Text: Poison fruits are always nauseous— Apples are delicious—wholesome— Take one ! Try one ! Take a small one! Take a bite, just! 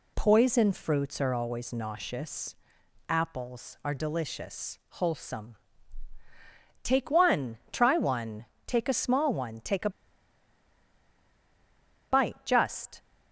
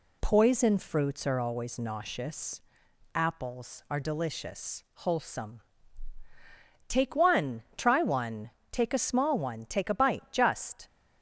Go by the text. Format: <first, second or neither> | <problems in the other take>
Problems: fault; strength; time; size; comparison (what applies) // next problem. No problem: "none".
second | pauses between "a" and "bite"; strong; at 9.8 s; 2.2 s long